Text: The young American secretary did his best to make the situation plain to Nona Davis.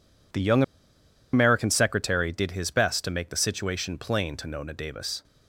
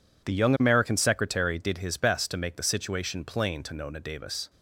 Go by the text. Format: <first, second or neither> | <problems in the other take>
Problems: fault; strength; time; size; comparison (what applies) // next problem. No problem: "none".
second | pauses between "young" and "American"; noticeable; at 0.6 s; 0.70 s long